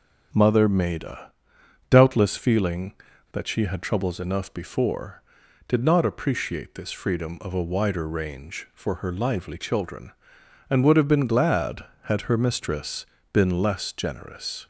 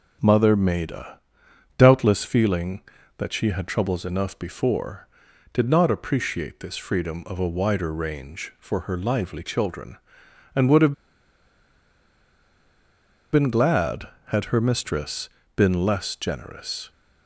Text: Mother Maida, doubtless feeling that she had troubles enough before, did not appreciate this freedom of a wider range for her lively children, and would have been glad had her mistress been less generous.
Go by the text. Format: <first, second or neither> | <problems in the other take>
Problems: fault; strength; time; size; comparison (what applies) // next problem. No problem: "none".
first | pauses between "have" and "been"; strong; at 10.9 s; 2.3 s long // pauses between "mistress" and "been"; slight; at 15.2 s; 0.26 s long; slight in the first